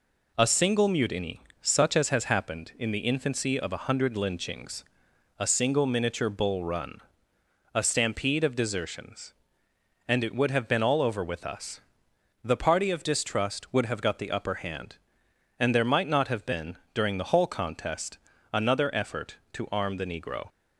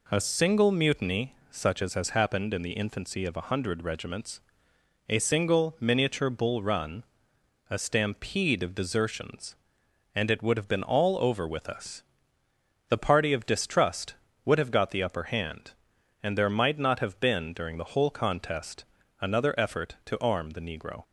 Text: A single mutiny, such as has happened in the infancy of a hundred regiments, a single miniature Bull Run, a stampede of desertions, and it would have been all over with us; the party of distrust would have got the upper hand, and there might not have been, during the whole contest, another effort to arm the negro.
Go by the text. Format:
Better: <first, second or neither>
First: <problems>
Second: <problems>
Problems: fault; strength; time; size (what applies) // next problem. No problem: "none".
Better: second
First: says "lynchings" for "regiments"; at 4.1 s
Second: none